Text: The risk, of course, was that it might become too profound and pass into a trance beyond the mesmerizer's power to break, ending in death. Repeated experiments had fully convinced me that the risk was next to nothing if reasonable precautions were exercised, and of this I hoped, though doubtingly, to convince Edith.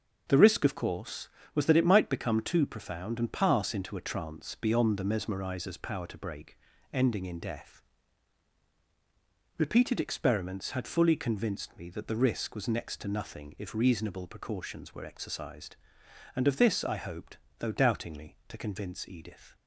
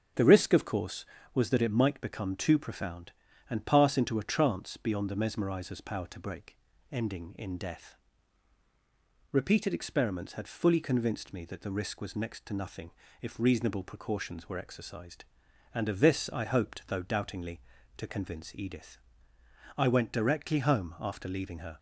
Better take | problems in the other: first | starts louder than the rest; strong; until 1.4 s; 7.5 dB; also in the first // pauses between "nothing" and "if"; slight; at 12.8 s; 0.32 s long // goes on to say "I went directly home after leaving her"; strong; from 19.7 s on; 2.0 s long

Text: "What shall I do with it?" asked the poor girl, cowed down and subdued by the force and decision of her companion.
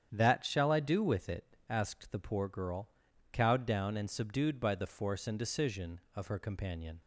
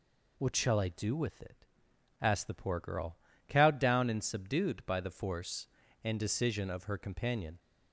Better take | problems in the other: second | starts louder than the rest; strong; until 1.1 s; 9 dB // says "That" for "What"; at 0.1 s

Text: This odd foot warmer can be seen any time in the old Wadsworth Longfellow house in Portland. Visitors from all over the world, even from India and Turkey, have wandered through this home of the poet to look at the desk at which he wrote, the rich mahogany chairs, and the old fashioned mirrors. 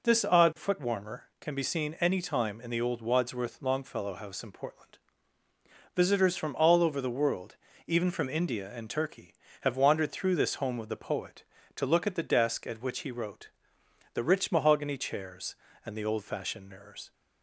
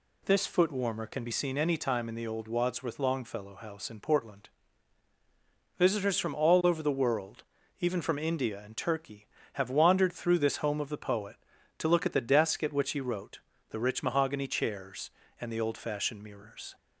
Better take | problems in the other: first | skips "odd"; at 0.4 s

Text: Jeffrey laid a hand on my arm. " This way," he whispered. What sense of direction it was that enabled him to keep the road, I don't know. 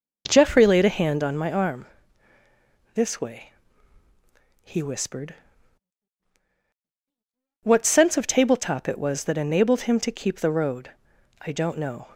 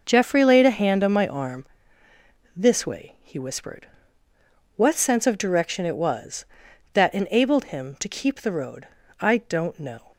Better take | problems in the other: second | says "tabletop" for "direction"; at 8.2 s

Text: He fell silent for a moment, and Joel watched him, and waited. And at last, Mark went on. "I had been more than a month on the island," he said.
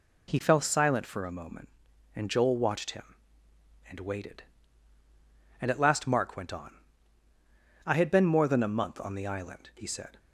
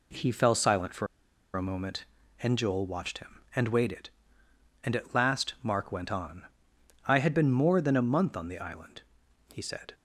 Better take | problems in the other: first | pauses between "for" and "a"; noticeable; at 1.0 s; 0.48 s long

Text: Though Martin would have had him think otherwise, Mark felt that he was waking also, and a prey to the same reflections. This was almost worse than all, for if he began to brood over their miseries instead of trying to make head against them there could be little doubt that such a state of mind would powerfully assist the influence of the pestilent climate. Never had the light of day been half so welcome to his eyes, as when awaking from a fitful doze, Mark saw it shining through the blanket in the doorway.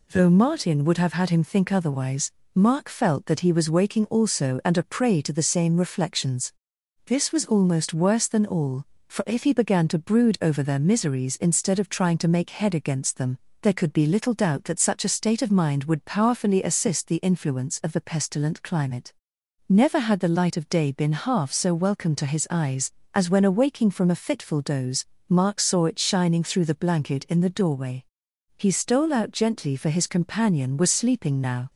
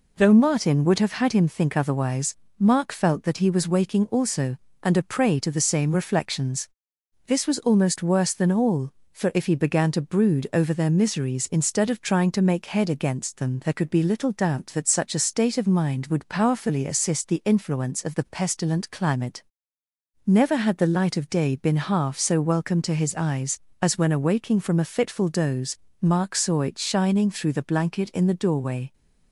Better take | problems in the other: second | pauses between "them" and "there"; slight; at 13.3 s; 0.24 s long // goes on to say "He stole out gently for his companion was sleeping now"; strong; from 28.5 s on; 3.1 s long

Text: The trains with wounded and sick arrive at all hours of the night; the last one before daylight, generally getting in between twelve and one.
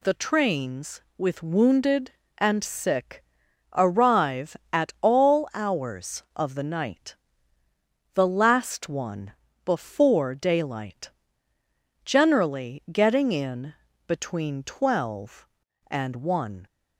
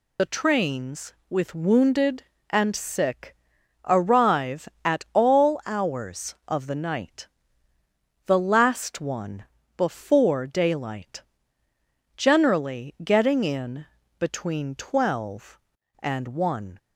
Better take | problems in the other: first | loses the start of "The"; at 0.1 s; 45 ms // pauses between "sick" and "arrive"; noticeable; at 3.3 s; 0.52 s long; noticeable in the first // pauses between "one" and "before"; slight; at 9.4 s; 0.30 s long; slight in the first // pauses between "in" and "between"; slight; at 13.8 s; 0.32 s long; slight in the first

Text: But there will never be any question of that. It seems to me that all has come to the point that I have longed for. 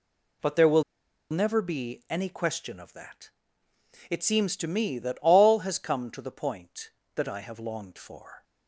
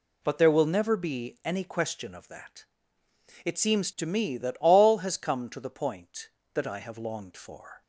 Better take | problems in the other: second | pauses between "will" and "never"; noticeable; at 0.8 s; 0.47 s long

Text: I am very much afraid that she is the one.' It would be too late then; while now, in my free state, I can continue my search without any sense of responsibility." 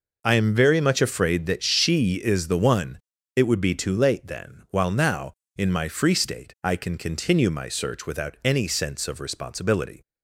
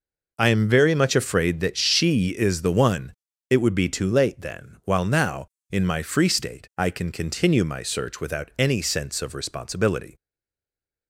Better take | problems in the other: first | stays silent after the last word; slight; from 10.1 s on; 0.9 s long

